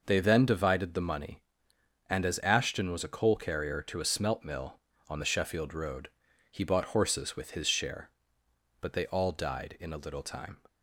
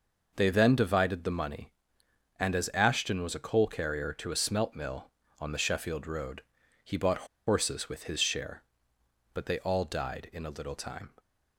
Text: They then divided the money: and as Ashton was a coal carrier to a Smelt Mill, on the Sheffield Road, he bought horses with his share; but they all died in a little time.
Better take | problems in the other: first | pauses between "bought" and "horses"; slight; at 7.2 s; 0.21 s long

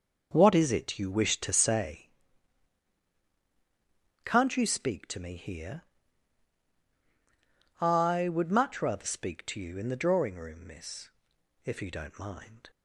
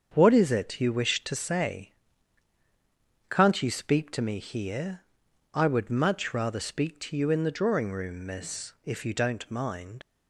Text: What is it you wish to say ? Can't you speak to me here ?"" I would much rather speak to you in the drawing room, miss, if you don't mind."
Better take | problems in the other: first | starts louder than the rest; until 1.1 s; 7 dB; also in the first // leaves "mind" unfinished; at 10.0 s; 45 ms

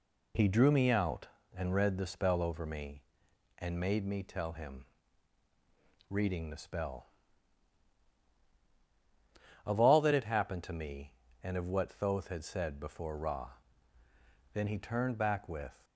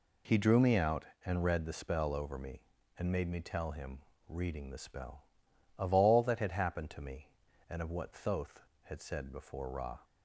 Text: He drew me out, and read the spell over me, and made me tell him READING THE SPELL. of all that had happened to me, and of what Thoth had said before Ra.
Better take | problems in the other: second | pauses between "him" and "READING"; strong; at 4.8 s; 1.2 s long; slight in the second // goes on to say "Then he turned back with"; from 14.5 s on; 1.3 s long

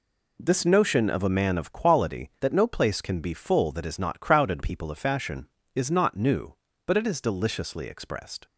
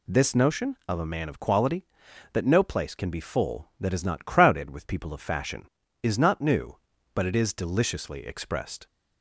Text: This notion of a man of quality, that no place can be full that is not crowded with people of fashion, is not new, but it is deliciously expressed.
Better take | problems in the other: second | skips "with"; at 4.6 s

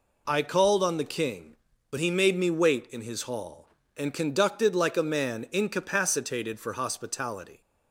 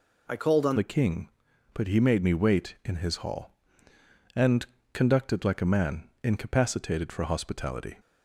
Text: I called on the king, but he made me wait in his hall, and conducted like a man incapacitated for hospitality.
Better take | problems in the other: first | changes voice at "the"; from 0.7 s on; 7.2 s long // pauses between "and" and "conducted"; slight; at 4.6 s; 0.26 s long

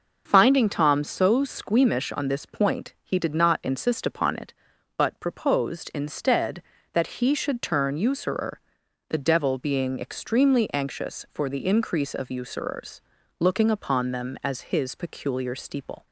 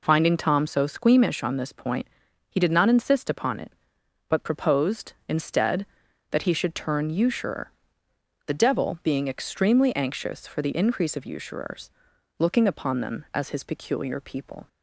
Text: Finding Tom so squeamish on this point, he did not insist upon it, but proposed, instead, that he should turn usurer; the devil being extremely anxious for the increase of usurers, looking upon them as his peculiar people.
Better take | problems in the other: second | says "steeple" for "people"; at 15.5 s

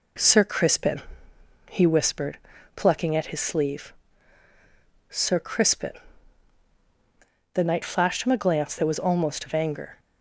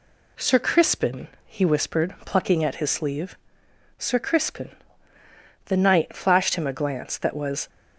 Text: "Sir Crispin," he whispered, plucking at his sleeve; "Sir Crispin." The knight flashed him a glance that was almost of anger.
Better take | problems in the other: first | stops before "almost of anger"; at 7.6 s

